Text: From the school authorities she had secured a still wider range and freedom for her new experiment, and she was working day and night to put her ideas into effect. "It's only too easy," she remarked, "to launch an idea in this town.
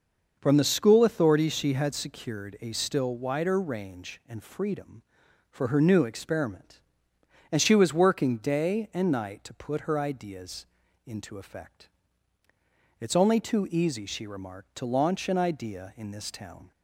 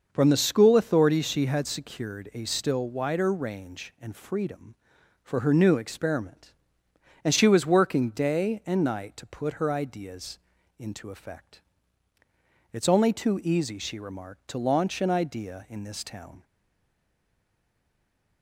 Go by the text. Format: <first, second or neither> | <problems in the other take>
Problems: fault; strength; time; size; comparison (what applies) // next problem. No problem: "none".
first | starts louder than the rest; noticeable; until 1.1 s; 6 dB; noticeable in the first // pauses between "ideas" and "into"; at 10.3 s; 0.40 s long; also in the first // stays silent after the last word; noticeable; from 16.4 s on; 2.0 s long